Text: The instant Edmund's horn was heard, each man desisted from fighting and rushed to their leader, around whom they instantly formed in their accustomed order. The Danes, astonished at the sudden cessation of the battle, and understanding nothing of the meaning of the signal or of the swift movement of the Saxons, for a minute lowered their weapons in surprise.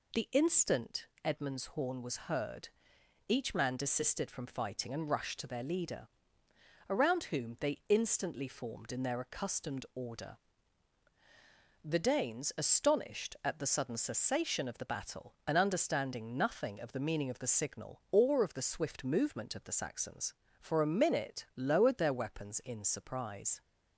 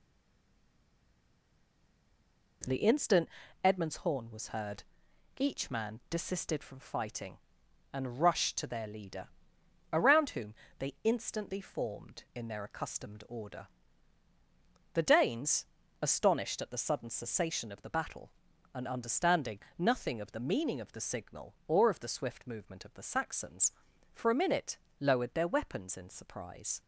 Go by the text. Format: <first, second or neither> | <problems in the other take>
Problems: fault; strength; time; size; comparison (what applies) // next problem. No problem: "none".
first | stays silent before the first word; strong; until 2.6 s; 2.6 s long // pauses between "instant" and "Edmund's"; slight; at 3.2 s; 0.36 s long; slight in the first // pauses between "whom" and "they"; slight; at 10.5 s; 0.24 s long // pauses between "understanding" and "nothing"; slight; at 19.5 s; 0.18 s long // pauses between "minute" and "lowered"; slight; at 24.7 s; 0.24 s long